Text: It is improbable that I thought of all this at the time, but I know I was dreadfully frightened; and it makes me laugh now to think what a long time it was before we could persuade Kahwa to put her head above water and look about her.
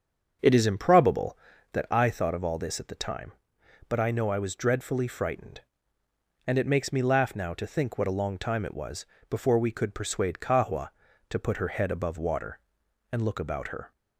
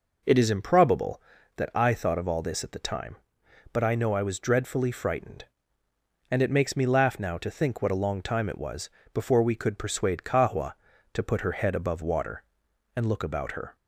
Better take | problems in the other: second | starts louder than the rest; until 2.2 s; 7 dB // pauses between "was" and "before"; slight; at 9.0 s; 0.24 s long; slight in the second

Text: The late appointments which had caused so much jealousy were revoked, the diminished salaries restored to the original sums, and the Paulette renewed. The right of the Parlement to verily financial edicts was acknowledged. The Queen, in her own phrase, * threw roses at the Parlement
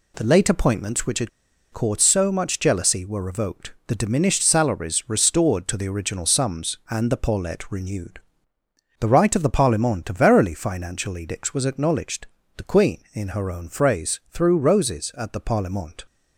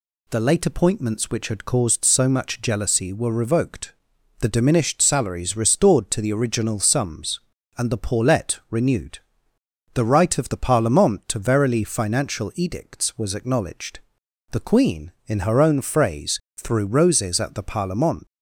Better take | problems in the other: second | pauses between "had" and "caused"; at 1.2 s; 0.42 s long

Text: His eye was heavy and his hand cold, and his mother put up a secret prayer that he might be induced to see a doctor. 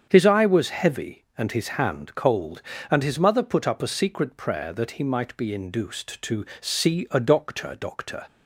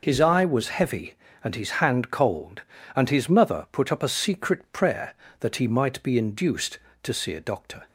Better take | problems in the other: second | starts louder than the rest; strong; until 1.1 s; 7.5 dB // pauses between "to" and "see"; slight; at 6.4 s; 0.16 s long // says "doctor" twice; at 7.7 s

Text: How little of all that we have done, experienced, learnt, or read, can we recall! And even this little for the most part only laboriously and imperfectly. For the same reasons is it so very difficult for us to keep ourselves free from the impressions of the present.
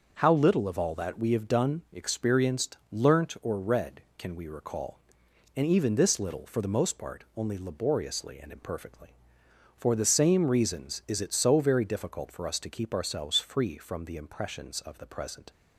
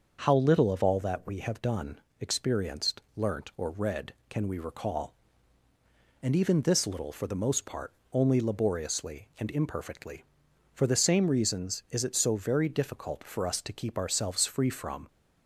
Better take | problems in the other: first | starts louder than the rest; until 1.2 s; 6.5 dB; also in the first // pauses between "part" and "only"; slight; at 7.9 s; 0.18 s long // stops before "the impressions of the present"; at 15.0 s

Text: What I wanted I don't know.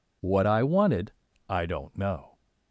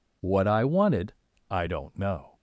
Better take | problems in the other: neither | pauses between "wanted" and "I"; slight; the same in both

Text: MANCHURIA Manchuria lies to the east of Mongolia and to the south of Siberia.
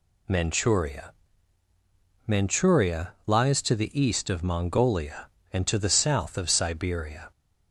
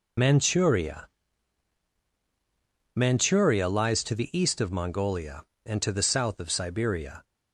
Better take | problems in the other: first | loses the start of "MANCHURIA"; at 0.1 s; 60 ms // pauses between "MANCHURIA" and "Manchuria"; strong; at 1.0 s; 1.8 s long; also in the first

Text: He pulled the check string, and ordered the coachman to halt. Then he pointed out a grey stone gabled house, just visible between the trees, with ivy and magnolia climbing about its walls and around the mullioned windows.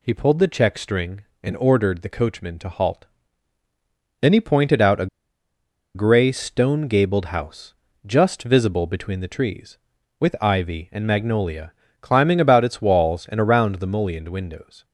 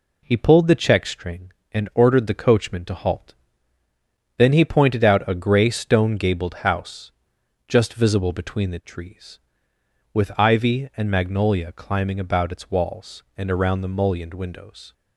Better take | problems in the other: second | pauses between "a" and "grey"; noticeable; at 5.0 s; 0.88 s long // pauses between "magnolia" and "climbing"; slight; at 11.7 s; 0.28 s long

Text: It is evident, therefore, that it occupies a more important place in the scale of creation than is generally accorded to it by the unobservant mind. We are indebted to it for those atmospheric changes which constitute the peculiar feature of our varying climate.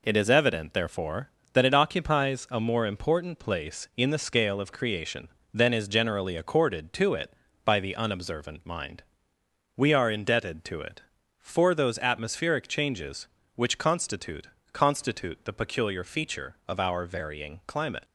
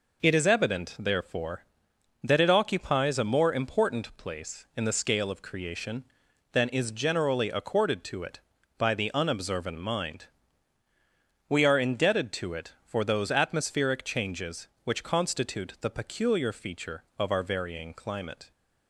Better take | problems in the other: second | says "constitute" twice; at 14.7 s

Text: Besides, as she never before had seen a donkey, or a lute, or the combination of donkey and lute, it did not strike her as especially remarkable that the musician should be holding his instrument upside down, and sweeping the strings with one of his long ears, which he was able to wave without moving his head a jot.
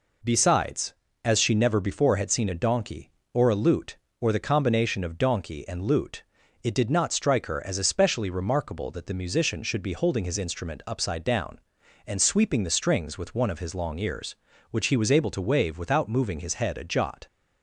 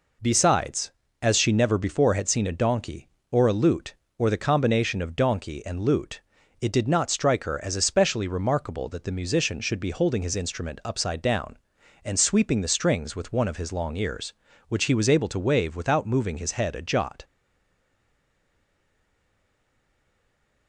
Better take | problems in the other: first | stays silent after the last word; strong; from 17.2 s on; 3.4 s long

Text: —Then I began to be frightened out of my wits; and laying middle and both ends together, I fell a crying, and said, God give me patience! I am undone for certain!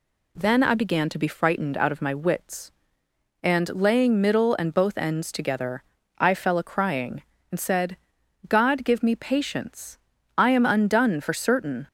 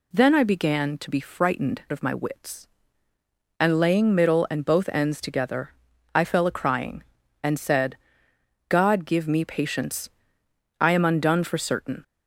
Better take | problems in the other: first | skips "out"; at 1.8 s

